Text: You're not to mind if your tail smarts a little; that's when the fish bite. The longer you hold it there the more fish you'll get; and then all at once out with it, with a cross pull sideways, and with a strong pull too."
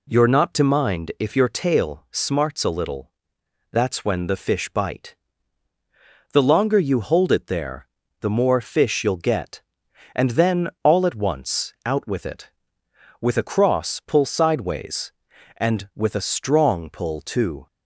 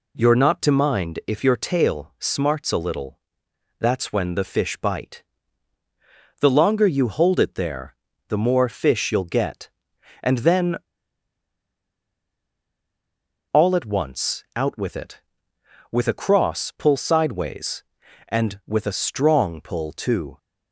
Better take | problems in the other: first | pauses between "there" and "the"; slight; at 7.9 s; 0.34 s long; slight in the first // pauses between "then" and "all"; strong; at 10.7 s; 2.7 s long

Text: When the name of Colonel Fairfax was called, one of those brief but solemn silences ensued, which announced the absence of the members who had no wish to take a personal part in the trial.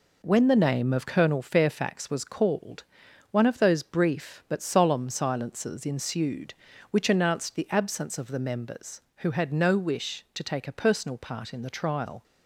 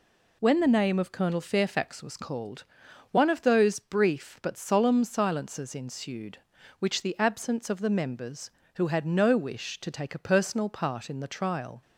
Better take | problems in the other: first | skips "announced"; at 7.0 s

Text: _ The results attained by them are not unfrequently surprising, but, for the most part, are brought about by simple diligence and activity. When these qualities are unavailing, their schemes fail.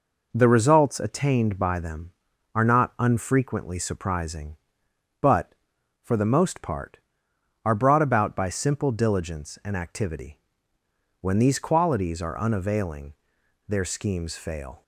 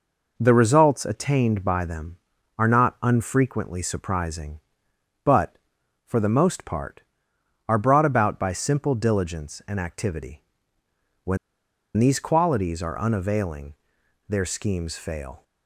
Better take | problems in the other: first | pauses between "When" and "these"; noticeable; at 11.3 s; 0.59 s long

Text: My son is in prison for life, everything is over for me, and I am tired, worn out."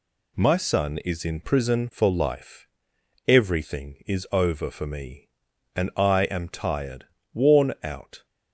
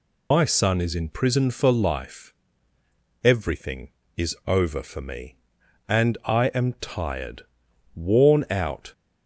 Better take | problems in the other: first | loses the start of "My"; at 0.3 s; 110 ms

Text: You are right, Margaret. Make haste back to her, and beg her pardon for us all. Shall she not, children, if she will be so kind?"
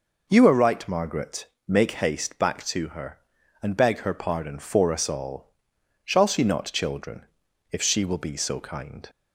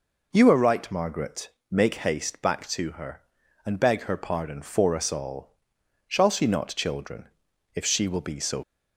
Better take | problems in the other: first | stops before "kind"; at 8.6 s

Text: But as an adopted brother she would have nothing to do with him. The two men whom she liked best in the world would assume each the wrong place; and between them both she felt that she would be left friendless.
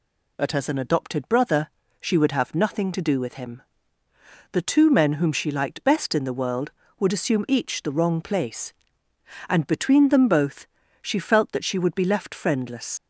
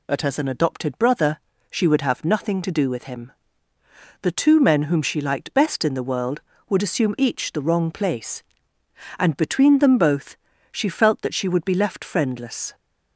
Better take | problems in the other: second | pauses between "brother" and "she"; slight; at 1.6 s; 0.32 s long; slight in the second // pauses between "both" and "she"; slight; at 10.6 s; 0.34 s long; slight in the second // leaves "friendless" unfinished; at 12.9 s; 75 ms

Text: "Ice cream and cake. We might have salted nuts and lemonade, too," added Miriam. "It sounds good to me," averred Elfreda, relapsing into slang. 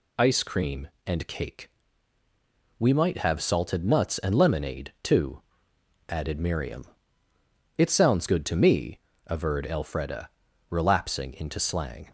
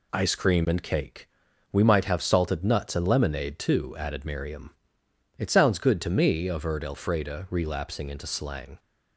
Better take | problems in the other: neither | none

